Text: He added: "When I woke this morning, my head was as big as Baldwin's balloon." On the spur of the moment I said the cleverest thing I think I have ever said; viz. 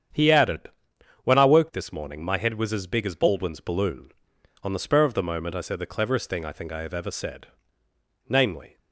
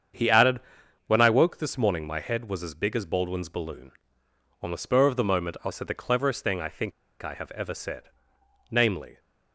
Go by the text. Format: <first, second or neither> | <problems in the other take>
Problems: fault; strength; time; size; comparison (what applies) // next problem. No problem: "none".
first | starts louder than the rest; strong; until 1.6 s; 7.5 dB; strong in the first // pauses between "think" and "I"; slight; at 6.9 s; 0.30 s long